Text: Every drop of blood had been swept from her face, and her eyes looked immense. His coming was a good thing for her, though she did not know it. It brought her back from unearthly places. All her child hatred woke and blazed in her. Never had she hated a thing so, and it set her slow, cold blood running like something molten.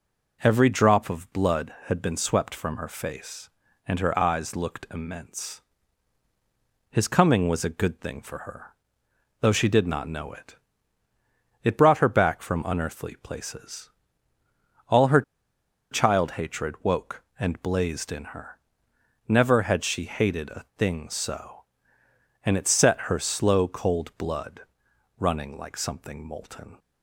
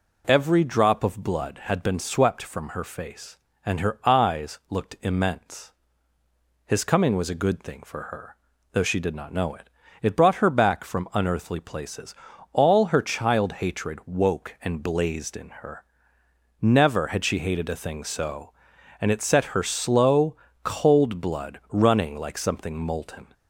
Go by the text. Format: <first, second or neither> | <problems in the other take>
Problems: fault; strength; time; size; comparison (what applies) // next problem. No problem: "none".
second | pauses between "her" and "child"; noticeable; at 15.2 s; 0.69 s long // pauses between "blood" and "running"; noticeable; at 24.6 s; 0.56 s long